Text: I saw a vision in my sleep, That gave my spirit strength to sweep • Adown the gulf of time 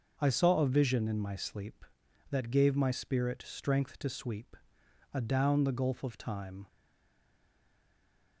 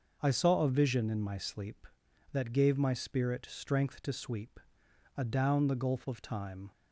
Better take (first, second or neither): second